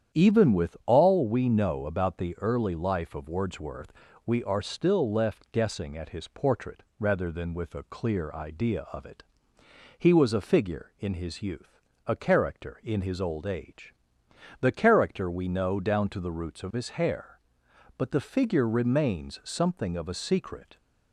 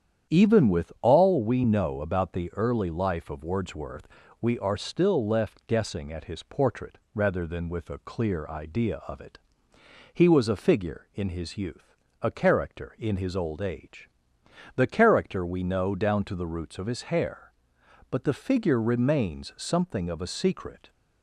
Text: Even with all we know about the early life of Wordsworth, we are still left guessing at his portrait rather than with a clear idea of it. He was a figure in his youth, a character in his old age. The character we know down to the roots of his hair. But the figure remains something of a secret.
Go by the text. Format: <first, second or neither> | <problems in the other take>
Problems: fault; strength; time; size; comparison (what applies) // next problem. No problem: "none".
neither | starts louder than the rest; strong; the same in both // pauses between "portrait" and "rather"; slight; the same in both